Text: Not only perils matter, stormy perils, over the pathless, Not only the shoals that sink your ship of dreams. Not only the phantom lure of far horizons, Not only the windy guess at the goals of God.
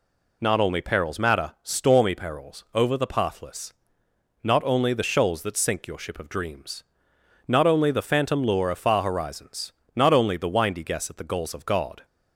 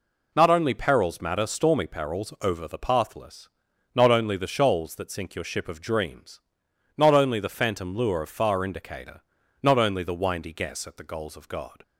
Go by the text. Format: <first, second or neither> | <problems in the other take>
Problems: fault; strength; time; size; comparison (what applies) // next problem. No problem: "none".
first | says "indicator" for "horizons"; at 8.6 s